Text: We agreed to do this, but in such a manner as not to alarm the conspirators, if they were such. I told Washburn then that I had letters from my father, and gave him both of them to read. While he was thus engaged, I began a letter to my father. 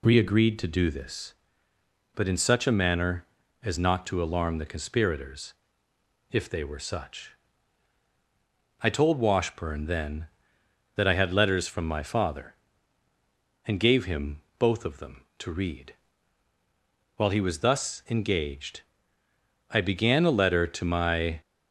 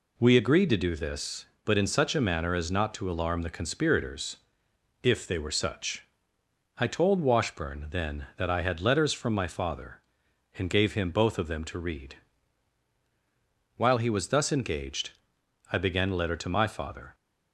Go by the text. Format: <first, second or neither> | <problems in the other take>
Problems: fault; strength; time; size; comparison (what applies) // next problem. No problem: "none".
second | pauses between "him" and "both"; slight; at 14.4 s; 0.18 s long // stops before "father"; at 21.4 s